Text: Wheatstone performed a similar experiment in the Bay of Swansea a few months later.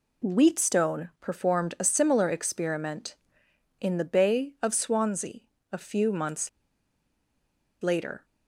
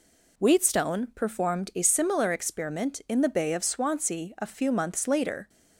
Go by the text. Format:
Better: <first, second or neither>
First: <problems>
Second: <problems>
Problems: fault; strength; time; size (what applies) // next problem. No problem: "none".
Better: second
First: pauses between "Swansea" and "a"; slight; at 5.4 s; 0.32 s long // pauses between "months" and "later"; strong; at 6.4 s; 1.3 s long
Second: none